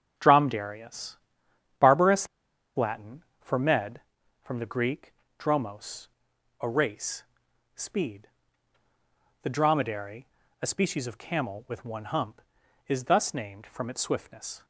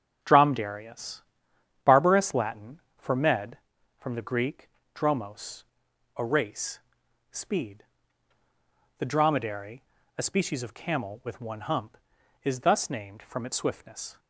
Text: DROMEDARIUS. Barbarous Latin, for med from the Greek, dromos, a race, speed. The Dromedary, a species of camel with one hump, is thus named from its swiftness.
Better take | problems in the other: second | starts louder than the rest; until 1.8 s; 7 dB; also in the second // pauses between "Barbarous" and "Latin"; noticeable; at 2.2 s; 0.50 s long

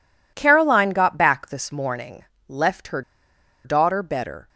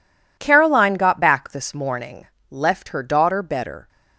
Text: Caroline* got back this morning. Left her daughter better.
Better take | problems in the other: second | pauses between "her" and "daughter"; noticeable; at 3.0 s; 0.63 s long

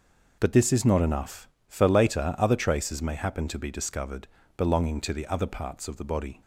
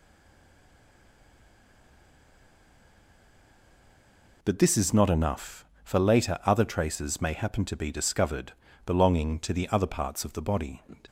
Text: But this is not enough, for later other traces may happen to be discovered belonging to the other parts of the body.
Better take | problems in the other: first | stays silent before the first word; strong; until 4.4 s; 4.4 s long // pauses between "discovered" and "belonging"; slight; at 8.5 s; 0.32 s long; slight in the first

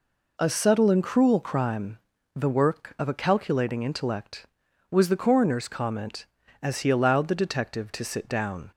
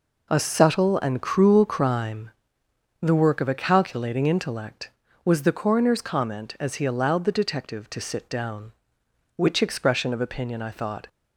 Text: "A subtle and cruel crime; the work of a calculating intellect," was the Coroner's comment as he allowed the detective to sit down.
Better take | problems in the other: first | goes on to say "Which expression of opinion I thought"; strong; from 9.3 s on; 1.7 s long

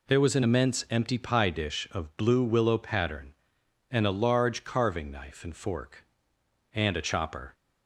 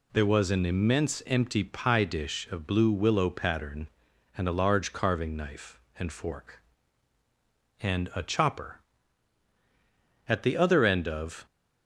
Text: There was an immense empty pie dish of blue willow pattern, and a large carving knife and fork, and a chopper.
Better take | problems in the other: first | goes on to say "At the other end of"; noticeable; from 10.2 s on; 1.1 s long

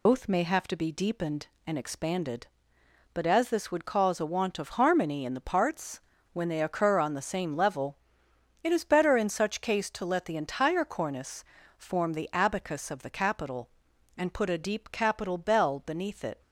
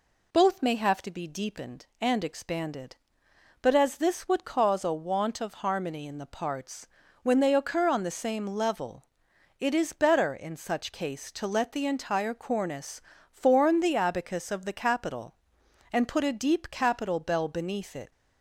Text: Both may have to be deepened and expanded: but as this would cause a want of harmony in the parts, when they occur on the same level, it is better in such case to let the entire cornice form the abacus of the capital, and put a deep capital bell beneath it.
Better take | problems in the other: second | loses the start of "Both"; at 0.0 s; 95 ms // pauses between "cornice" and "form"; slight; at 11.4 s; 0.34 s long; slight in the second

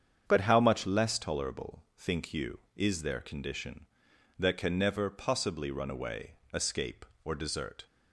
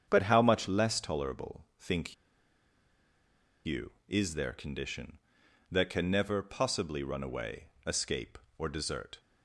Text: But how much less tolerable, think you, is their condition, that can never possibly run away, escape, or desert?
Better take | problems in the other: first | starts louder than the rest; strong; until 1.0 s; 8 dB; strong in the first // pauses between "think" and "you"; strong; at 2.1 s; 1.5 s long

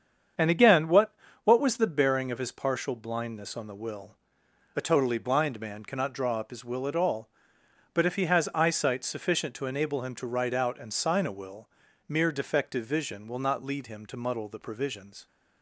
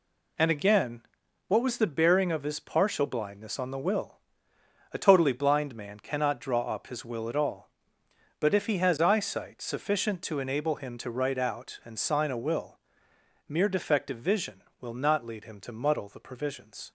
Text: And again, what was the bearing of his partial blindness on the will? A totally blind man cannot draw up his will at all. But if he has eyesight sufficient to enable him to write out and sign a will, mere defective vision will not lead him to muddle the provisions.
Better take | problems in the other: second | starts louder than the rest; strong; until 1.6 s; 7.5 dB // says "what" twice; at 1.4 s

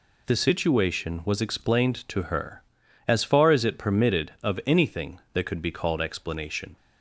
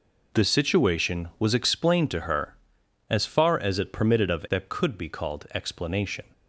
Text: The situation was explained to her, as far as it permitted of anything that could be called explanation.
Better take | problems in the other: first | skips "anything"; at 4.4 s

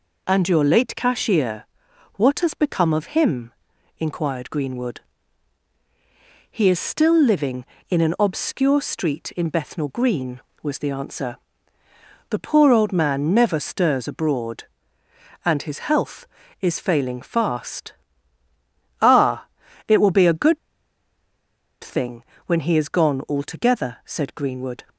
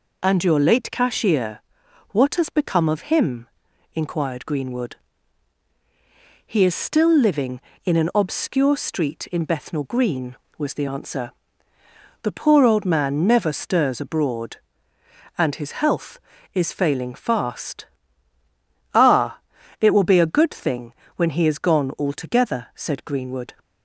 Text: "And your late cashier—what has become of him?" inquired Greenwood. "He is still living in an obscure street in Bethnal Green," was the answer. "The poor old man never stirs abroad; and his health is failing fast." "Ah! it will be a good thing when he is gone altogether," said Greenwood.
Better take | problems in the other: second | pauses between "good" and "thing"; strong; at 20.5 s; 1.2 s long // pauses between "thing" and "when"; slight; at 22.2 s; 0.24 s long; slight in the second

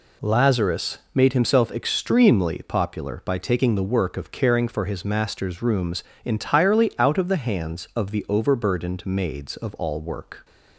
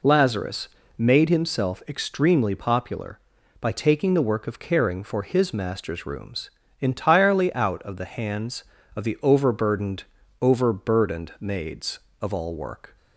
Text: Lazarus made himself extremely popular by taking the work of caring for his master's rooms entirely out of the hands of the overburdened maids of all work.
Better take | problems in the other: first | pauses between "Lazarus" and "made"; slight; at 0.6 s; 0.30 s long; slight in the first // pauses between "rooms" and "entirely"; slight; at 6.4 s; 0.30 s long; slight in the first // says "overburdened" twice; at 10.3 s

